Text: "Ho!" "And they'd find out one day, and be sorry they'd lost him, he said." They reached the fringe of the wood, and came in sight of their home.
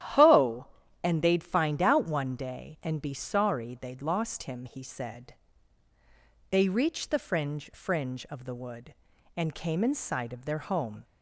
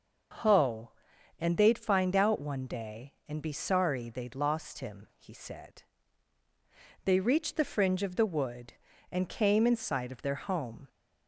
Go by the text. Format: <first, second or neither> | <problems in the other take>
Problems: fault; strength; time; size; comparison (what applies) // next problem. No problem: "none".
second | starts louder than the rest; strong; until 1.5 s; 11.5 dB // says "fringe" twice; at 7.7 s